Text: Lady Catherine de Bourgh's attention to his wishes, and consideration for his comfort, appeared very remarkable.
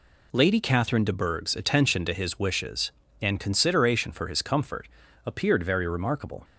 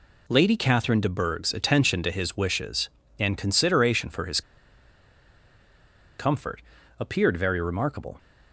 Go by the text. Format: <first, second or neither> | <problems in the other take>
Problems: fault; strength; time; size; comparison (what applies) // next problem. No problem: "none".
first | pauses between "his" and "comfort"; strong; at 4.4 s; 1.7 s long